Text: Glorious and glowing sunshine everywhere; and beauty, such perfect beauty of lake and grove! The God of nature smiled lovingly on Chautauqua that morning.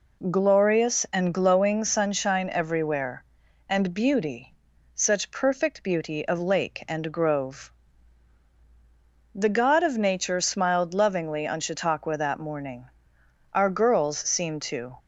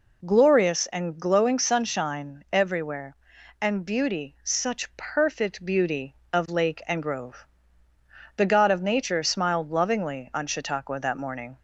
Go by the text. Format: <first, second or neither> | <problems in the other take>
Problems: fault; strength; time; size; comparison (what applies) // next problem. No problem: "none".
second | goes on to say "Our girls seemed to"; from 13.5 s on; 1.4 s long